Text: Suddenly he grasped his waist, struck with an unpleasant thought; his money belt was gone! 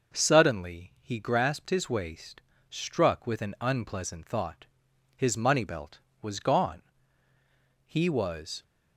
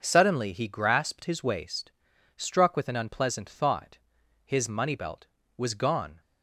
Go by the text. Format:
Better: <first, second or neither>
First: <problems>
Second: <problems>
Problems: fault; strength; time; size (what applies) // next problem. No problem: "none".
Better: second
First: goes on to say "He was"; noticeable; from 7.8 s on; 0.76 s long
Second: none